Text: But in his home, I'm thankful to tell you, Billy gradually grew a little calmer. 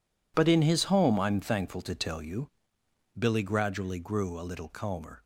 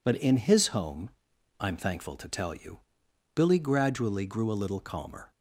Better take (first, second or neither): neither